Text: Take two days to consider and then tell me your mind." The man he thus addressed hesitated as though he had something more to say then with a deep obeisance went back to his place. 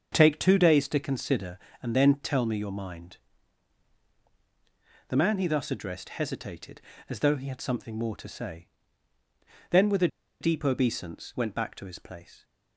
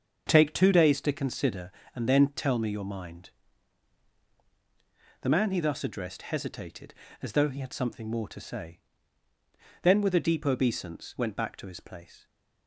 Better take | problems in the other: second | starts louder than the rest; strong; until 1.1 s; 7 dB; strong in the second // pauses between "say" and "then"; at 8.6 s; 1.0 s long; also in the second // pauses between "a" and "deep"; slight; at 10.0 s; 0.33 s long

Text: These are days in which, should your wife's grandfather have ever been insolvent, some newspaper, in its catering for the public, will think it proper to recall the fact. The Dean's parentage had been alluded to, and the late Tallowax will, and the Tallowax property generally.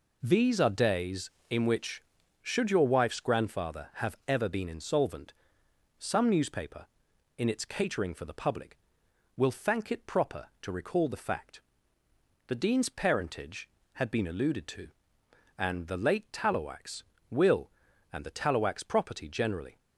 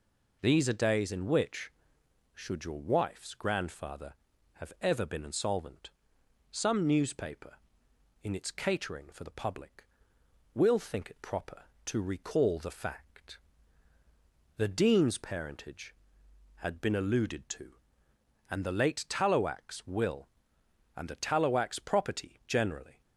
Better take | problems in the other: second | says "thank" for "think"; at 9.5 s

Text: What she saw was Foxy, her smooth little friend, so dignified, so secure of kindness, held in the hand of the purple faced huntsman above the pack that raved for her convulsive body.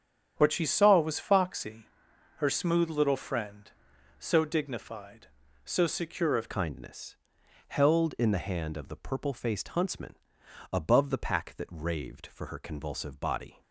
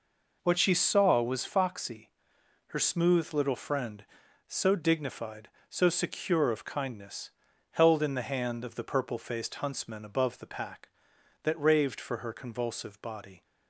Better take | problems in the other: second | starts louder than the rest; strong; until 1.3 s; 8.5 dB // changes voice at "kindness"; from 6.4 s on; 7.2 s long // pauses between "huntsman" and "above"; noticeable; at 10.1 s; 0.56 s long

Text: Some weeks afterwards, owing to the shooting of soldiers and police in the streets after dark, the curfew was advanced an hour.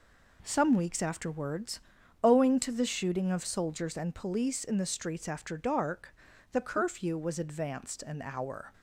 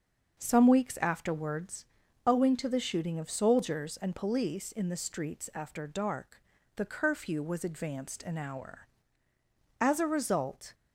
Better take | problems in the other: first | starts louder than the rest; until 1.4 s; 6.5 dB // goes on to say "As a result"; noticeable; from 9.8 s on; 0.94 s long

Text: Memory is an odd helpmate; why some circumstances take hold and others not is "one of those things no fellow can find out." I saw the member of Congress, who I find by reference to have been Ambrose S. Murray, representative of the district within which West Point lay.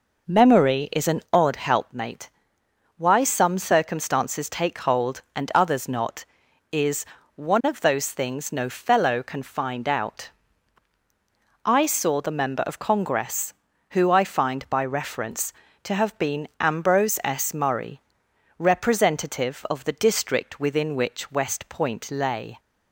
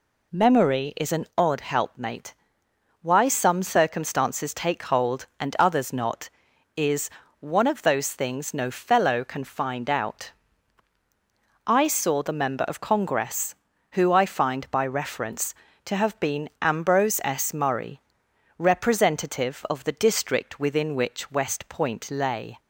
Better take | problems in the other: second | starts louder than the rest; noticeable; until 1.9 s; 5 dB // pauses between "is" and "one"; slight; at 7.0 s; 0.32 s long; slight in the second

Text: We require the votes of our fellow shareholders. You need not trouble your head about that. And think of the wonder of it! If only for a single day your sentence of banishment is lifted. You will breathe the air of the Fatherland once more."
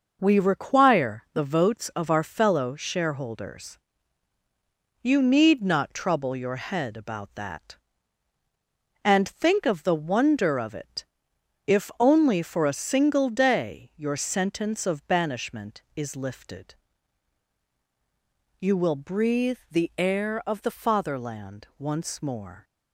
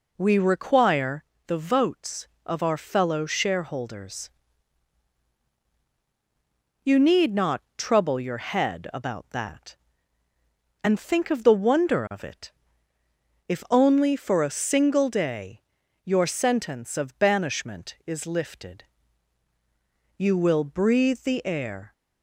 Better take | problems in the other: first | pauses between "require" and "the"; slight; at 1.2 s; 0.22 s long // pauses between "not" and "trouble"; slight; at 7.6 s; 0.16 s long // pauses between "day" and "your"; at 15.6 s; 0.44 s long // stops before "of the Fatherland once more"; at 21.9 s

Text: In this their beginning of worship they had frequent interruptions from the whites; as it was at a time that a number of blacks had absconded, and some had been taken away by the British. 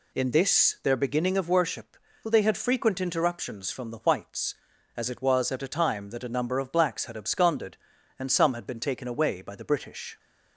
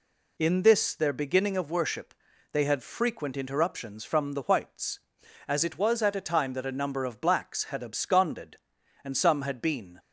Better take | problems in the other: first | pauses between "worship" and "they"; at 2.1 s; 0.38 s long; slight in the first // stops before "taken away by the British"; at 9.9 s

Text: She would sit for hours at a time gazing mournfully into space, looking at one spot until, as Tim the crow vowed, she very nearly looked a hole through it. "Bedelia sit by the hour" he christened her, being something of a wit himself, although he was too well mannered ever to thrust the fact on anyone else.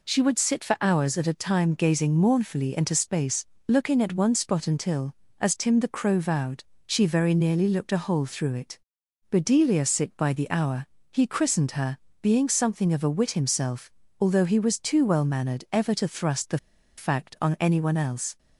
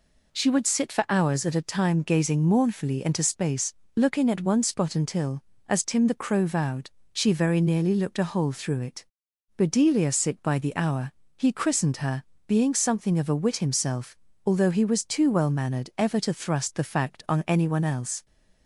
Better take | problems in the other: second | pauses between "hour" and "he"; slight; at 10.8 s; 0.24 s long; slight in the second // pauses between "the" and "fact"; at 16.5 s; 0.39 s long

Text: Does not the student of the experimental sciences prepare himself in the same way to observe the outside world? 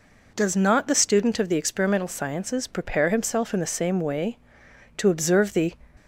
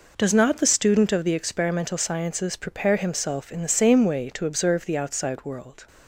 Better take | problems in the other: second | stops before "outside world"; at 5.9 s

